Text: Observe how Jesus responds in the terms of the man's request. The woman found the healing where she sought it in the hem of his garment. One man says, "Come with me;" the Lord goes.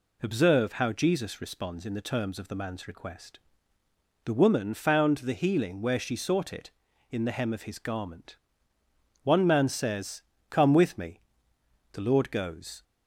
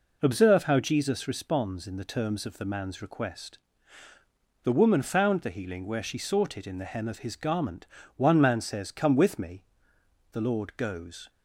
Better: neither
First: none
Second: none

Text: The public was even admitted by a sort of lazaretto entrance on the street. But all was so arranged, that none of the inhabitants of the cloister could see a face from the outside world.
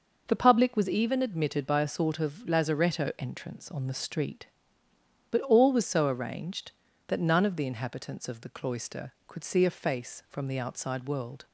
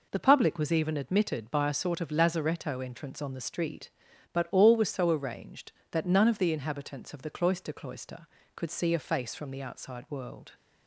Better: first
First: none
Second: says "cloister" twice; at 7.7 s

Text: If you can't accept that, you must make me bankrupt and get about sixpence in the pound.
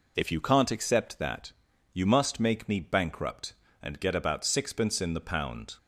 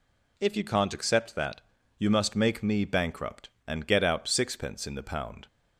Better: first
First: none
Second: says "out" for "about"; at 4.0 s

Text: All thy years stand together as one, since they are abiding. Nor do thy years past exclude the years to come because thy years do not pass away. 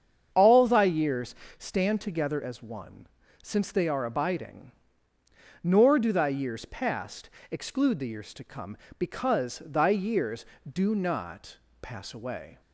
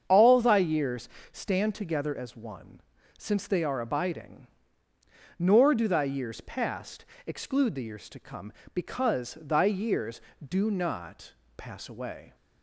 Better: neither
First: starts louder than the rest; strong; until 1.3 s; 7.5 dB // pauses between "years" and "stand"; slight; at 1.3 s; 0.24 s long // pauses between "past" and "exclude"; slight; at 7.2 s; 0.22 s long // pauses between "not" and "pass"; slight; at 11.5 s; 0.24 s long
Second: starts louder than the rest; strong; until 1.0 s; 7.5 dB // pauses between "years" and "stand"; slight; at 1.0 s; 0.24 s long // pauses between "past" and "exclude"; slight; at 7.0 s; 0.22 s long // pauses between "not" and "pass"; slight; at 11.3 s; 0.24 s long

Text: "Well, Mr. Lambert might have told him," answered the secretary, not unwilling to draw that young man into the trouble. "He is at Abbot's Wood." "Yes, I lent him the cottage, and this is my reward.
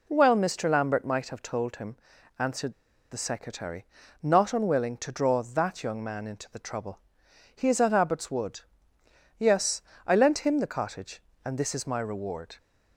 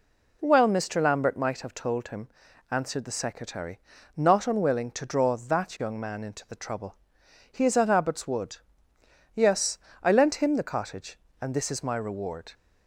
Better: second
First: pauses between "answered" and "the"; at 2.7 s; 0.38 s long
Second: none

